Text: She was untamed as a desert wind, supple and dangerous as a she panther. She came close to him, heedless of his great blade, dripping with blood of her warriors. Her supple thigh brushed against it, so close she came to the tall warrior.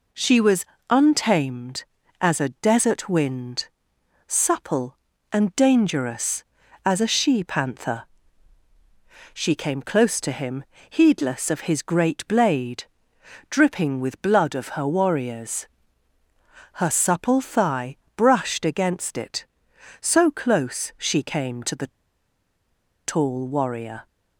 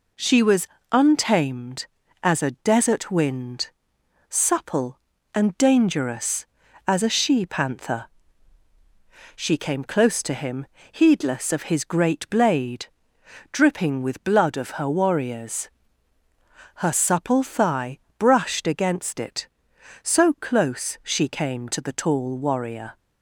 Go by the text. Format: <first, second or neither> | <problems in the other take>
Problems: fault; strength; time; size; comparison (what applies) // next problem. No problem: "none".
second | pauses between "was" and "untamed"; slight; at 0.6 s; 0.24 s long; slight in the second // pauses between "thigh" and "brushed"; slight; at 17.9 s; 0.22 s long; slight in the second // pauses between "the" and "tall"; at 21.8 s; 1.1 s long